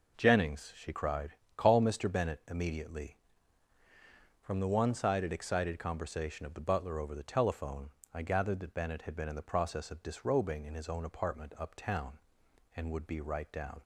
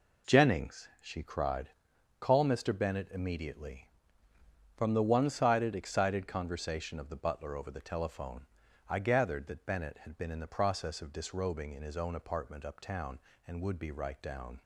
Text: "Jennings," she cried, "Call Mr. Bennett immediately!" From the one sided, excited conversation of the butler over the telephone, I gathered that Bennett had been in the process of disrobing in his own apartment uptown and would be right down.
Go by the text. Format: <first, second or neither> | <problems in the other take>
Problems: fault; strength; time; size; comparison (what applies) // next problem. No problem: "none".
neither | none